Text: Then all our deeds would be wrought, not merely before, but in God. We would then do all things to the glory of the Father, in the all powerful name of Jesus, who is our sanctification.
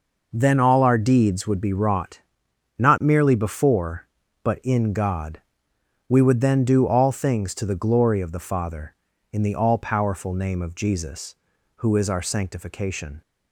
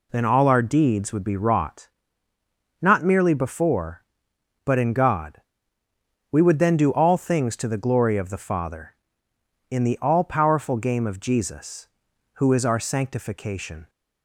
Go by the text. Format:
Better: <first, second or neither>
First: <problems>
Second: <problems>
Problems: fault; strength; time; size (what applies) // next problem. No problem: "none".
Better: first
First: none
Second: says "game" for "name"; at 10.7 s